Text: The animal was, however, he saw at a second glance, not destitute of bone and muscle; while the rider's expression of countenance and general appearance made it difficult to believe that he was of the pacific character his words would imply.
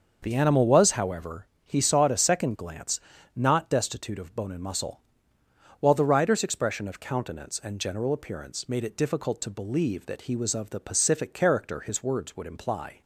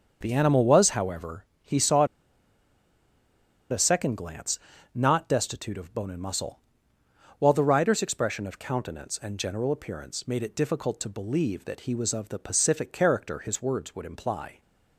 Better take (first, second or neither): first